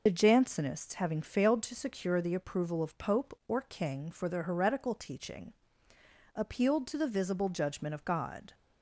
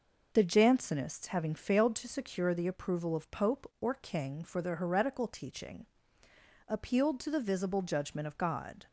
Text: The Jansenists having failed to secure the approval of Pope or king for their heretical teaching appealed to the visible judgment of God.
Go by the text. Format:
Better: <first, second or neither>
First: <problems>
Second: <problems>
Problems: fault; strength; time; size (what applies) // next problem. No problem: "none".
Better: second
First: loses the start of "The"; at 0.0 s; 50 ms // pauses between "teaching" and "appealed"; noticeable; at 5.5 s; 0.80 s long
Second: pauses between "teaching" and "appealed"; noticeable; at 5.8 s; 0.80 s long